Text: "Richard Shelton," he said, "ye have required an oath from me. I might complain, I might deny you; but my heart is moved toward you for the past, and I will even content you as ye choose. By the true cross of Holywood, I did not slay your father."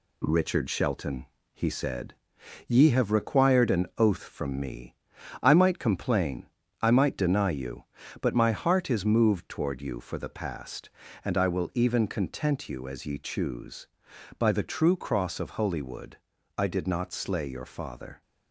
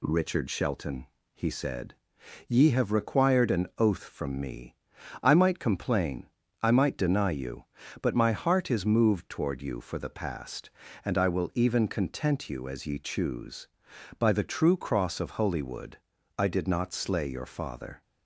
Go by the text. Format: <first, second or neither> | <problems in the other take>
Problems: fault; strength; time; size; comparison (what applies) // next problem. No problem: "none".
second | gets quieter; noticeable; throughout; 4 dB